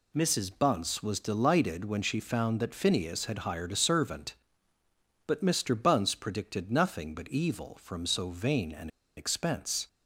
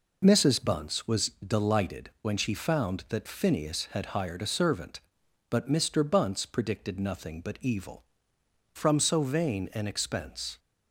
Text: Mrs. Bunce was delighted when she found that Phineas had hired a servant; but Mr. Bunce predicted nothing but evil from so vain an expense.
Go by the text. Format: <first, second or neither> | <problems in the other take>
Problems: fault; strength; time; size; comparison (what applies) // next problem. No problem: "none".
second | pauses between "an" and "expense"; slight; at 8.8 s; 0.28 s long